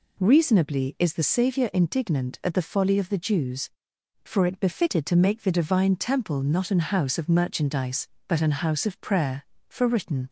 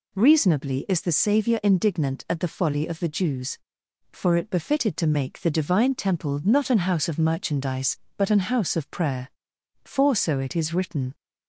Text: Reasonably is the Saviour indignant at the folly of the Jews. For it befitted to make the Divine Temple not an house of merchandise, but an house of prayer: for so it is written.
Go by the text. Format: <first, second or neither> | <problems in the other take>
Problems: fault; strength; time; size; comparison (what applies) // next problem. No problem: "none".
second | skips "so it is"; at 9.8 s